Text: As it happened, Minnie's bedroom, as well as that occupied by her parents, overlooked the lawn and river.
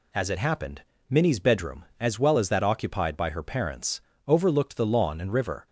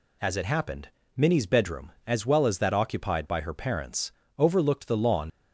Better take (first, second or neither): first